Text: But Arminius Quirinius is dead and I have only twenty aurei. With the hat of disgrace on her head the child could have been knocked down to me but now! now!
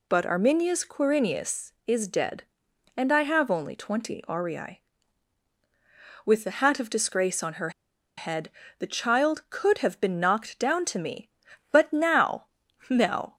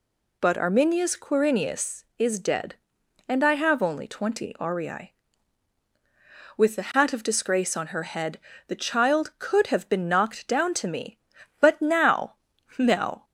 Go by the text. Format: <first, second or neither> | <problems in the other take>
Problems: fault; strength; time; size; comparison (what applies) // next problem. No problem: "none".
second | pauses between "her" and "head"; noticeable; at 7.7 s; 0.46 s long // pauses between "head" and "the"; slight; at 8.4 s; 0.30 s long; slight in the second